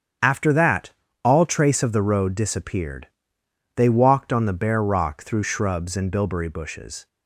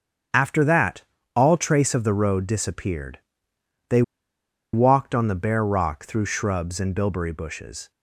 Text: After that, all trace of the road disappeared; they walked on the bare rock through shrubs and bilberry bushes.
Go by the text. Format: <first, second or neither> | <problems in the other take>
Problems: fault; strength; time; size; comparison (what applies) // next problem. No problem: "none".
first | starts louder than the rest; strong; until 1.6 s; 8.5 dB; strong in the first // pauses between "they" and "walked"; noticeable; at 4.0 s; 0.71 s long